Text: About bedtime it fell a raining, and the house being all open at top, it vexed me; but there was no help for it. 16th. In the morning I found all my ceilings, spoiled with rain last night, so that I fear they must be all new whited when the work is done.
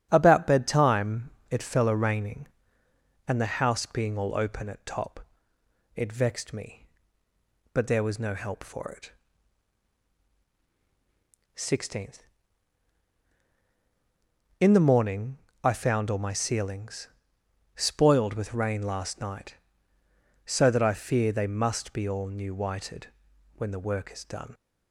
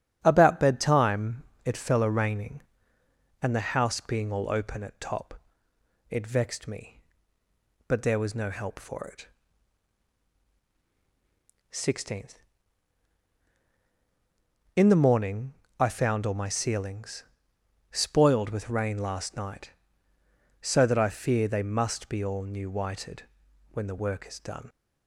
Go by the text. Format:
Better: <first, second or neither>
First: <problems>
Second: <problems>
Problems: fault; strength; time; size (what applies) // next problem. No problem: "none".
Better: neither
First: starts louder than the rest; strong; until 1.1 s; 9 dB // pauses between "bedtime" and "it"; slight; at 1.2 s; 0.22 s long // pauses between "morning" and "I"; slight; at 15.3 s; 0.26 s long // pauses between "whited" and "when"; noticeable; at 23.0 s; 0.48 s long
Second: starts louder than the rest; strong; until 1.2 s; 9 dB // pauses between "bedtime" and "it"; slight; at 1.4 s; 0.24 s long // pauses between "morning" and "I"; slight; at 15.5 s; 0.26 s long // pauses between "whited" and "when"; noticeable; at 23.2 s; 0.48 s long